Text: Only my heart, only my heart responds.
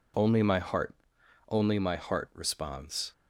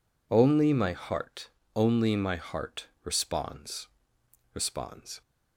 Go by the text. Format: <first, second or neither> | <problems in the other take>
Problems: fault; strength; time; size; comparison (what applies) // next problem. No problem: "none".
first | pauses between "heart" and "responds"; slight; at 2.8 s; 0.16 s long // says "responds" twice; at 4.5 s